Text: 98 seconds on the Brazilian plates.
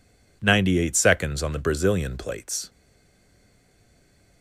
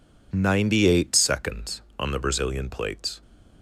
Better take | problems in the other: second | stays silent after the last word; noticeable; from 2.6 s on; 1.8 s long

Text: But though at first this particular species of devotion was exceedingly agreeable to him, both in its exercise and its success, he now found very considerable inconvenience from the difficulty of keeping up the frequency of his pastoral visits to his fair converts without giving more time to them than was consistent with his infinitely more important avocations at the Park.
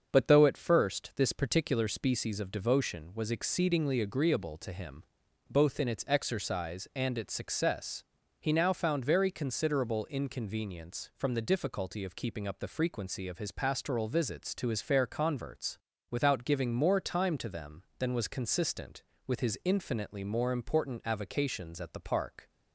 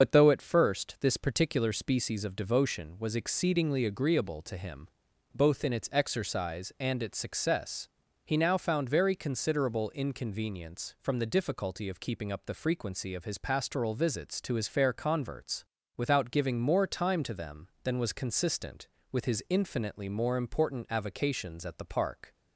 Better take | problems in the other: first | loses the start of "But"; at 0.0 s; 40 ms // starts louder than the rest; until 1.0 s; 6.5 dB; also in the first // pauses between "converts" and "without"; slight; at 15.6 s; 0.32 s long; slight in the first

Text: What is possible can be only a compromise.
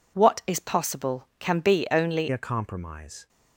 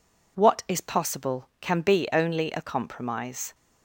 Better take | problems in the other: second | changes voice at "a"; from 2.3 s on; 0.9 s long

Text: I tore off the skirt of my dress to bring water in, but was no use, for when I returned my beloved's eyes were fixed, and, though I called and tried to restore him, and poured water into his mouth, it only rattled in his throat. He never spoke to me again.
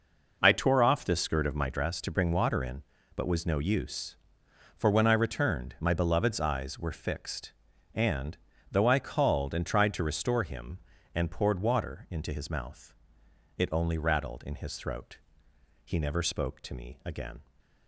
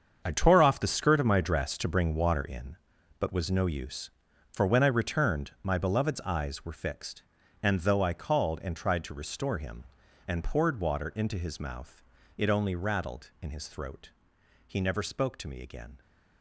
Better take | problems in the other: first | gets quieter; strong; throughout; 12.5 dB

